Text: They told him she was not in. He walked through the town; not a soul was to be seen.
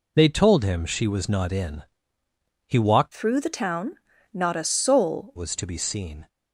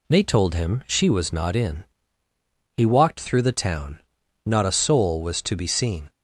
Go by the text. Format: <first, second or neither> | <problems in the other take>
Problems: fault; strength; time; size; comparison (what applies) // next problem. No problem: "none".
second | changes voice from "through" to "soul"; from 3.1 to 5.3 s; 2.2 s long